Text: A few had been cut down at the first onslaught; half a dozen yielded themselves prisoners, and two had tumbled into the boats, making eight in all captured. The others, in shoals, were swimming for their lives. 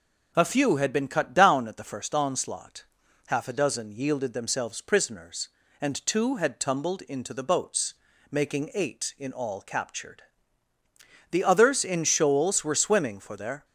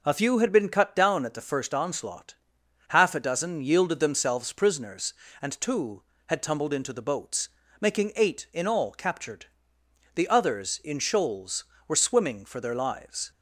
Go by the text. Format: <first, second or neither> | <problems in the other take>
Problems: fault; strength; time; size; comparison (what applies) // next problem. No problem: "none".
second | stops before "lives"; at 13.6 s